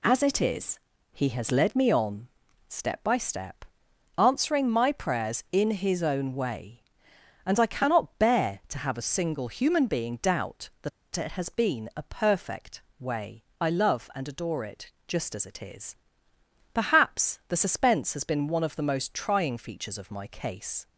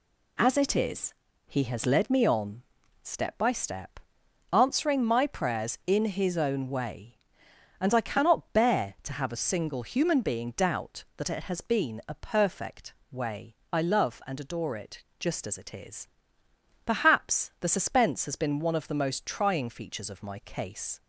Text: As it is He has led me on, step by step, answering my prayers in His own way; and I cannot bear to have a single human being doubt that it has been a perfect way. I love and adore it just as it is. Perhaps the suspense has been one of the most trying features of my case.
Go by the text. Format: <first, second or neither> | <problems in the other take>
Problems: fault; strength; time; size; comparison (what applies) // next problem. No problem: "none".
second | pauses between "is" and "He"; slight; at 0.7 s; 0.34 s long; slight in the second // pauses between "that" and "it"; slight; at 10.9 s; 0.25 s long // pauses between "perfect" and "way"; slight; at 12.8 s; 0.16 s long; slight in the second // pauses between "it" and "just"; slight; at 14.8 s; 0.16 s long; slight in the second